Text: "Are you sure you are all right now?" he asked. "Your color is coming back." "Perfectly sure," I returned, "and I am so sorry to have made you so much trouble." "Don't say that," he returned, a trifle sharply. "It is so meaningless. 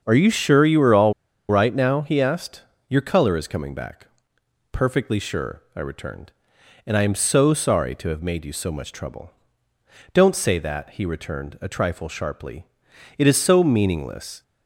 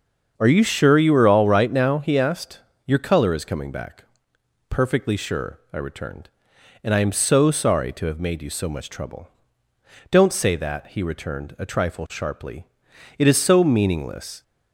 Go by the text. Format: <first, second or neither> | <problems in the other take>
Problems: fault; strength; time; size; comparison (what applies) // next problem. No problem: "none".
second | starts louder than the rest; until 1.0 s; 6.5 dB; also in the second // pauses between "all" and "right"; at 1.1 s; 0.37 s long